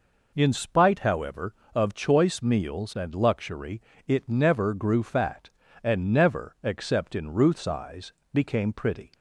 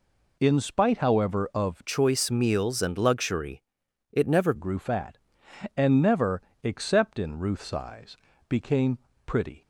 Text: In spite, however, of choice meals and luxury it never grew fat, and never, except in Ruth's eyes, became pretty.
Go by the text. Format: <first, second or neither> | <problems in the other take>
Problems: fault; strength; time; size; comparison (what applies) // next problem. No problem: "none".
first | changes voice from "choice" to "never"; from 1.8 to 4.5 s; 2.7 s long // pauses between "luxury" and "it"; noticeable; at 3.6 s; 0.50 s long; slight in the first // pauses between "became" and "pretty"; slight; at 8.9 s; 0.30 s long